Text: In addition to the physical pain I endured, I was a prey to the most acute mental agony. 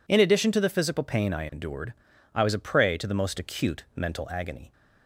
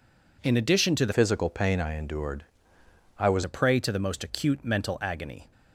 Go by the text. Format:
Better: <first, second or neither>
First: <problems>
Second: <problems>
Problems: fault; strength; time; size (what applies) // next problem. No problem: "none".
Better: first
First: none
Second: changes voice from "physical" to "was"; from 1.1 to 3.4 s; 2.3 s long